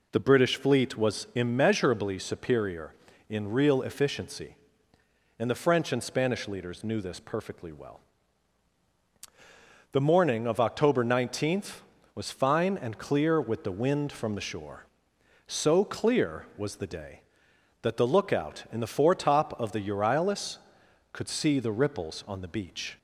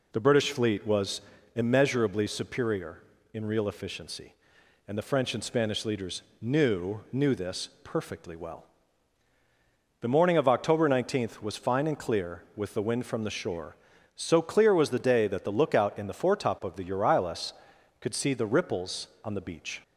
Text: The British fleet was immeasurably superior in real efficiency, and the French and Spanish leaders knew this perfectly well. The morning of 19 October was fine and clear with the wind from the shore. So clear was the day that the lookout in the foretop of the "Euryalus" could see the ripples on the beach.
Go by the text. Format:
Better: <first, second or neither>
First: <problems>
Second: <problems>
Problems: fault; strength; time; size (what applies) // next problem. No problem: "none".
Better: first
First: none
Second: pauses between "was" and "immeasurably"; slight; at 1.2 s; 0.32 s long // pauses between "leaders" and "knew"; slight; at 6.2 s; 0.20 s long // says "knew" twice; at 7.1 s